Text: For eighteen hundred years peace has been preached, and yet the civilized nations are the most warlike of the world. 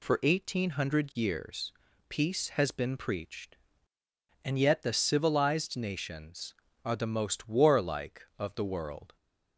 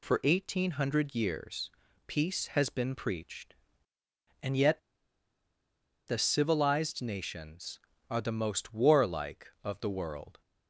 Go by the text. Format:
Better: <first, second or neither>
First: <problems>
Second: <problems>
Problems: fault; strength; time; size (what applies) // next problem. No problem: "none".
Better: first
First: pauses between "years" and "peace"; at 1.7 s; 0.38 s long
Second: pauses between "years" and "peace"; at 1.6 s; 0.38 s long // pauses between "yet" and "the"; strong; at 4.8 s; 1.2 s long